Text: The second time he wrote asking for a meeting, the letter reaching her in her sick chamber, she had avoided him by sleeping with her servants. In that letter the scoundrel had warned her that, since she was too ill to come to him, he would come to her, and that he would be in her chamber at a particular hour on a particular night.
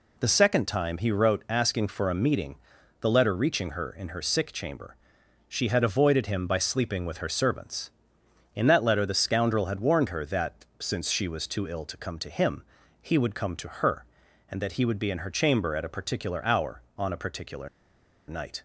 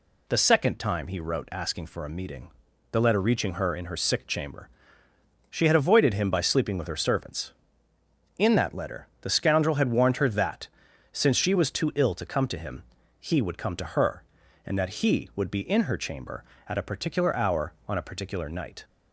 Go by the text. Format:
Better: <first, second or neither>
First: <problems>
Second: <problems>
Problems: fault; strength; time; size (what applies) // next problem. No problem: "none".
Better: second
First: pauses between "particular" and "night"; noticeable; at 17.6 s; 0.59 s long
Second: none